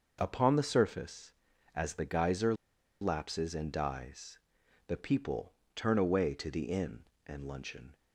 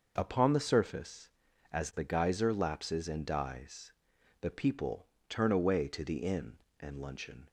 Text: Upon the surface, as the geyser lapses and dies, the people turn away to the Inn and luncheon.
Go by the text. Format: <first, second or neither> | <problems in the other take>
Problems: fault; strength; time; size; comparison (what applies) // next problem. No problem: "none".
second | pauses between "geyser" and "lapses"; noticeable; at 2.5 s; 0.47 s long // pauses between "people" and "turn"; slight; at 5.5 s; 0.22 s long; slight in the second